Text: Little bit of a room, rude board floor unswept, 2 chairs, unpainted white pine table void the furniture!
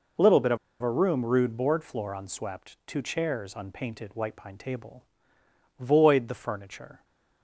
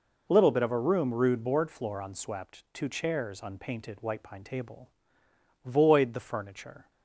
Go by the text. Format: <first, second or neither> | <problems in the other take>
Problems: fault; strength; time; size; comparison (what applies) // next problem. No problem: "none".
second | pauses between "of" and "a"; slight; at 0.5 s; 0.24 s long // pauses between "table" and "void"; noticeable; at 5.0 s; 0.76 s long; noticeable in the second